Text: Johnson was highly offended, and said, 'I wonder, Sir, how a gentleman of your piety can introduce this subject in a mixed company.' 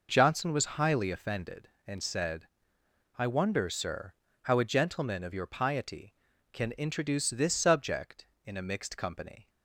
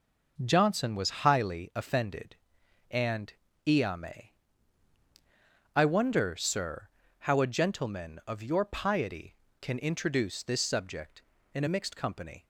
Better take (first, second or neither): first